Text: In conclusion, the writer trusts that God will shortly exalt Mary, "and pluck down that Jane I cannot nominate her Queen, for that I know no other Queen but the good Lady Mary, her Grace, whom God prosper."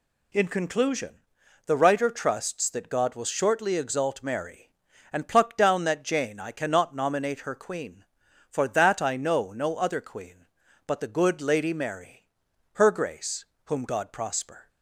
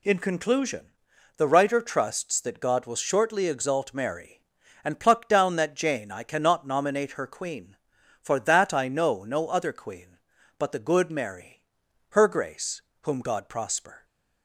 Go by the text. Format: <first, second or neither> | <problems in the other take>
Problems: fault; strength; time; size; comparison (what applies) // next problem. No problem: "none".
first | skips "Lady"; at 11.1 s